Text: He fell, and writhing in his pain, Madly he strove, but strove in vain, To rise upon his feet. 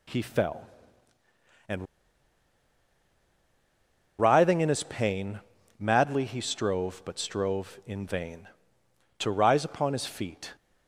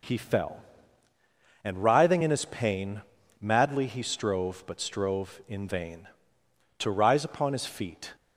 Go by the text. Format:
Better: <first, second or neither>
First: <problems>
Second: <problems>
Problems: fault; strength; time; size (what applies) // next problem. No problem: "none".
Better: second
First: pauses between "and" and "writhing"; strong; at 1.8 s; 2.3 s long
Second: none